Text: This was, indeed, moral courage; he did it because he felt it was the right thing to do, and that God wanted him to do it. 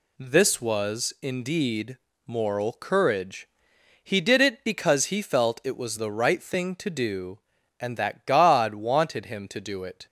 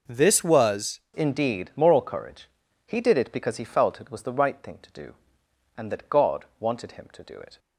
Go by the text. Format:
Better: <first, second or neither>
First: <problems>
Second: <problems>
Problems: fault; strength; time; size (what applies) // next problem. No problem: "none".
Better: first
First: none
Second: changes voice at "indeed"; from 1.1 s on; 6.4 s long